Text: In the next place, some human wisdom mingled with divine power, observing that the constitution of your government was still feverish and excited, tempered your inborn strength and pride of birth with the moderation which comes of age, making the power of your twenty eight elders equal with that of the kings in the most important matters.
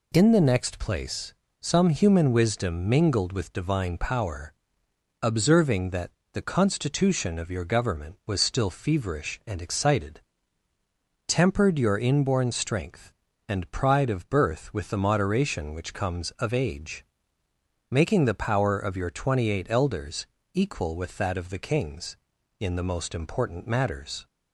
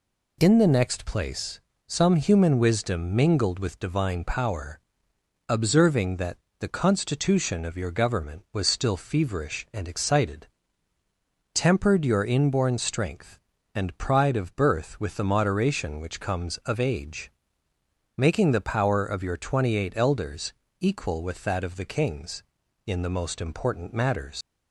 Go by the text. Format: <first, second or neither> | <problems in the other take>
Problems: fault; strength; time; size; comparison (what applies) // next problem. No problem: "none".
first | pauses between "that" and "the"; slight; at 6.3 s; 0.22 s long; slight in the first // pauses between "elders" and "equal"; slight; at 20.5 s; 0.26 s long; slight in the first // leaves "matters" unfinished; at 24.4 s; 125 ms